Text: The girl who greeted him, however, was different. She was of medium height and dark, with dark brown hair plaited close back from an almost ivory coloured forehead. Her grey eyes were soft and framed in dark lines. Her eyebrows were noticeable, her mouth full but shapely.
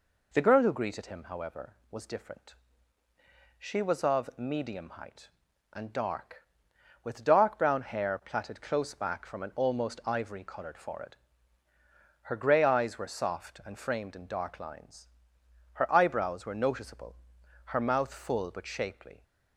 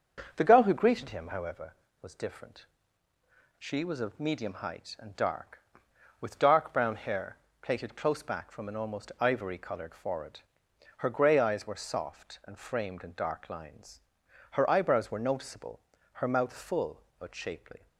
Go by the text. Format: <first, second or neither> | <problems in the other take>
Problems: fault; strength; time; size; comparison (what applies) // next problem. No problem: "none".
first | starts louder than the rest; until 1.6 s; 6.5 dB // pauses between "hair" and "plaited"; slight; at 7.3 s; 0.24 s long